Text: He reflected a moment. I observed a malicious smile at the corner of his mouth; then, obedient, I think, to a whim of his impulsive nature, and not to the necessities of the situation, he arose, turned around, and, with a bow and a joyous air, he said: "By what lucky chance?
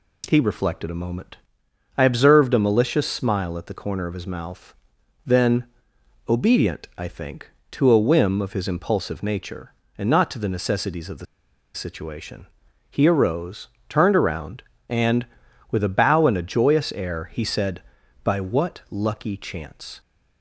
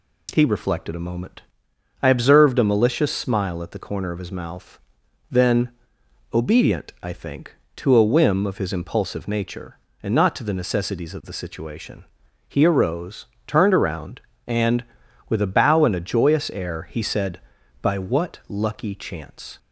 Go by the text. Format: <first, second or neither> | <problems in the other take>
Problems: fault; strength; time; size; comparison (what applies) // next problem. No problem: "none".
second | pauses between "the" and "situation"; noticeable; at 11.2 s; 0.50 s long